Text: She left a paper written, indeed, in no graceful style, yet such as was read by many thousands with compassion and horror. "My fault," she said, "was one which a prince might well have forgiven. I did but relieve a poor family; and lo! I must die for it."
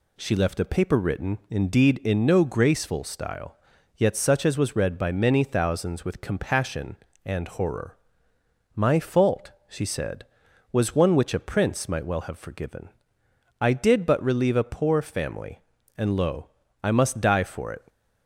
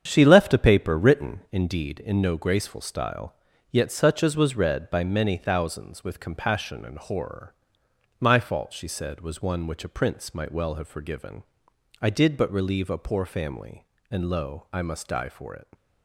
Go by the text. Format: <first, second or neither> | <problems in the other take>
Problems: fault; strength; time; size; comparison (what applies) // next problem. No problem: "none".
first | starts louder than the rest; strong; until 1.7 s; 8 dB